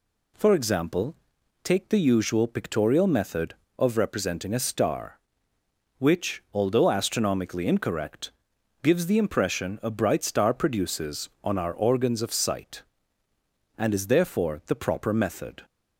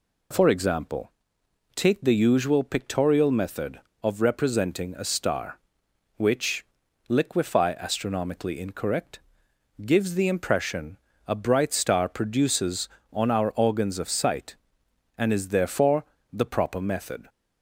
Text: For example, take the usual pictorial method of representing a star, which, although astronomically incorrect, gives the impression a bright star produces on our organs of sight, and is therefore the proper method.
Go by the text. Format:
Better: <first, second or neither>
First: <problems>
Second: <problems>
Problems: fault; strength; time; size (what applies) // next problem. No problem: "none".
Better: first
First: none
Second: says "liquefy" for "although"; at 7.0 s // pauses between "impression" and "a"; slight; at 10.9 s; 0.32 s long // pauses between "therefore" and "the"; slight; at 16.0 s; 0.26 s long